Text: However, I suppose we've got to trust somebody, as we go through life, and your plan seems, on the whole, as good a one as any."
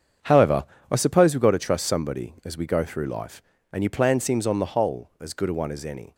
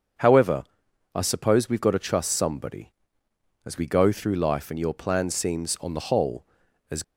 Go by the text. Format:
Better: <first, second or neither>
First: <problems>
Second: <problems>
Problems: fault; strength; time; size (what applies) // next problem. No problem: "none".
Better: first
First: starts louder than the rest; strong; until 1.4 s; 7.5 dB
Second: starts louder than the rest; until 1.7 s; 6.5 dB // stops before "good a one as any"; at 7.0 s